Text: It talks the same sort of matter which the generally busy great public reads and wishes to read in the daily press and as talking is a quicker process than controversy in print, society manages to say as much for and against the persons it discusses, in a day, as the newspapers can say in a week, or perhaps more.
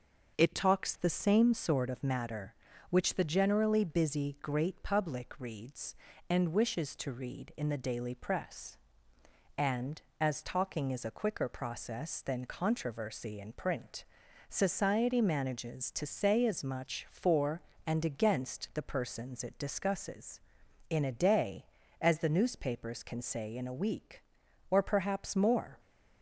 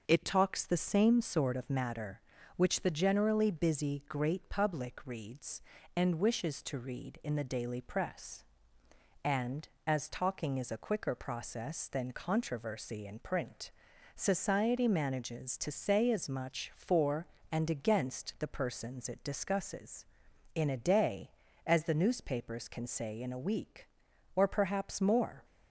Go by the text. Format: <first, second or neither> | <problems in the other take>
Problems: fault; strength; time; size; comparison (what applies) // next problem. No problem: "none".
neither | starts louder than the rest; the same in both